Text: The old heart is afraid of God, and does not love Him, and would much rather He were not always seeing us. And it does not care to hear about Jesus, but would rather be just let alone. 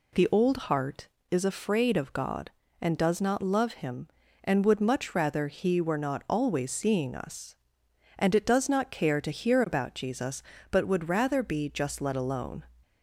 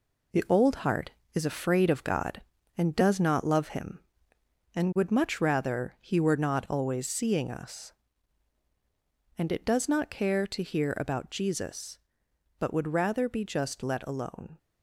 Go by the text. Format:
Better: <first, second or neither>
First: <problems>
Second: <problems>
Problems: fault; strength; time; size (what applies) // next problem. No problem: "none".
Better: first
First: none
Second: gets quieter; throughout; 6.5 dB